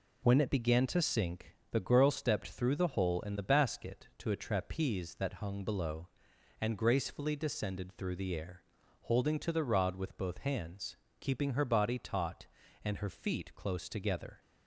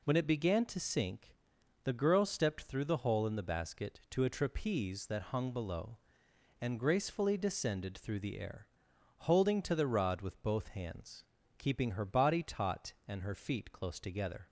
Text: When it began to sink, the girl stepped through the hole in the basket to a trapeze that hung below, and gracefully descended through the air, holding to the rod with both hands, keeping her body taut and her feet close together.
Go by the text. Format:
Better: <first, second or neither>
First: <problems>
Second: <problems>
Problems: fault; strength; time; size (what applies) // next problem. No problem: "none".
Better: neither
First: none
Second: none